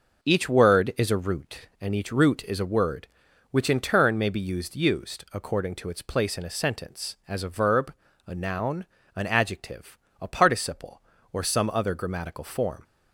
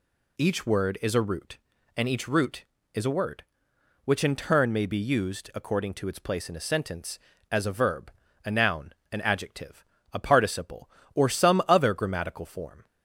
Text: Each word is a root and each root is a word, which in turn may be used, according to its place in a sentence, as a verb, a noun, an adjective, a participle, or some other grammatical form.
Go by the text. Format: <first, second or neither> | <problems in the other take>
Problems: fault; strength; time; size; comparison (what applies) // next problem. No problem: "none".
second | says "used" twice; at 4.7 s